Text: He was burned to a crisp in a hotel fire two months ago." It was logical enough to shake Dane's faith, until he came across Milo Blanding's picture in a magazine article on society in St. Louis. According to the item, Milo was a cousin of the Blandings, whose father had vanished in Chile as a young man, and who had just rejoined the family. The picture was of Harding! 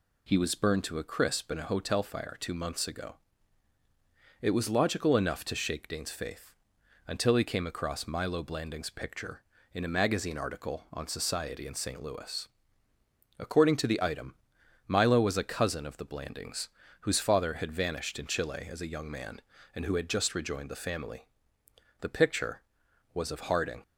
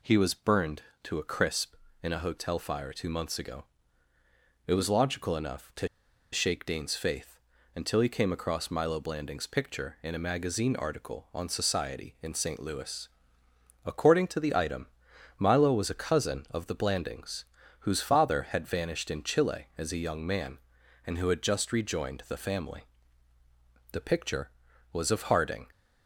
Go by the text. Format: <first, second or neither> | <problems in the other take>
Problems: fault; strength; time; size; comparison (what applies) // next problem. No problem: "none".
first | pauses between "to" and "shake"; noticeable; at 5.8 s; 0.46 s long